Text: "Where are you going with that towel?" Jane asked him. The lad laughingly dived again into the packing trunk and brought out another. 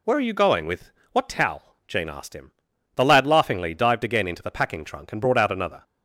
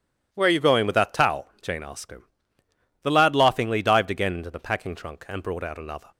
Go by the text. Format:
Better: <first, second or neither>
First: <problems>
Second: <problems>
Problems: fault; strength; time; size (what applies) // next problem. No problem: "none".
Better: second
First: says "what" for "that"; at 1.1 s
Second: none